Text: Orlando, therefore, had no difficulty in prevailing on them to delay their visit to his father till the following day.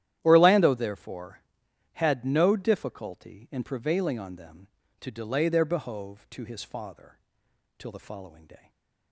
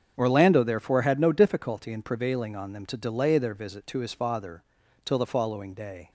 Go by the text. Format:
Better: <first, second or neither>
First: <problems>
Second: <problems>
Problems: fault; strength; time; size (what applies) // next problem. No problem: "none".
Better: second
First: starts louder than the rest; strong; until 1.2 s; 11.5 dB // says "behove" for "visit"; at 5.6 s // pauses between "father" and "till"; noticeable; at 7.1 s; 0.60 s long // stays silent after the last word; slight; from 8.5 s on; 0.6 s long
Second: starts louder than the rest; strong; until 1.1 s; 7 dB // pauses between "father" and "till"; at 4.6 s; 0.42 s long